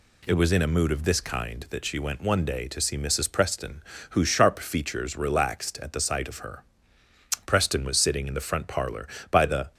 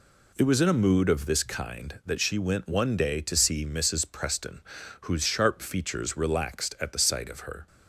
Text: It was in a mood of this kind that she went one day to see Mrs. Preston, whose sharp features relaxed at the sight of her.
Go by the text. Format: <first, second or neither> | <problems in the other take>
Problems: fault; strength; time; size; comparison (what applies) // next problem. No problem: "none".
second | goes on to say "Preston was sitting in the front parlor by the"; strong; from 7.4 s on; 2.2 s long